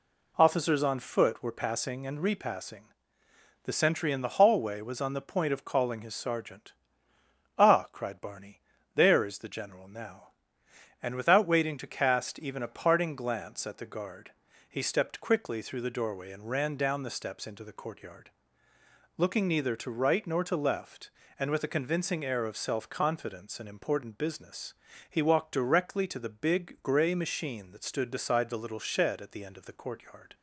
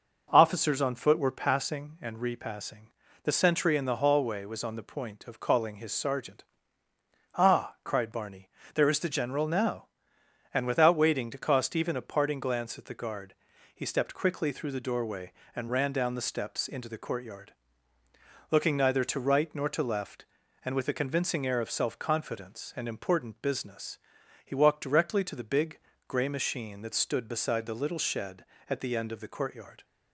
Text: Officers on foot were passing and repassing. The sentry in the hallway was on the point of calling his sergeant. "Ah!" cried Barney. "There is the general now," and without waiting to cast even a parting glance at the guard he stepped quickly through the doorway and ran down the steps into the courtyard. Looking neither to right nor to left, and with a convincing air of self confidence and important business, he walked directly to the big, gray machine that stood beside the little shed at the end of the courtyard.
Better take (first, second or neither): first